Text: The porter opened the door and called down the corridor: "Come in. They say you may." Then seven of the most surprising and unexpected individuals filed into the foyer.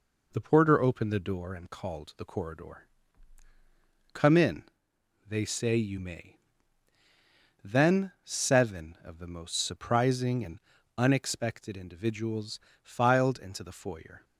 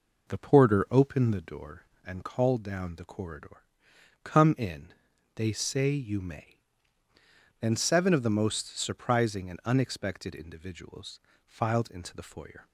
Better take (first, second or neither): second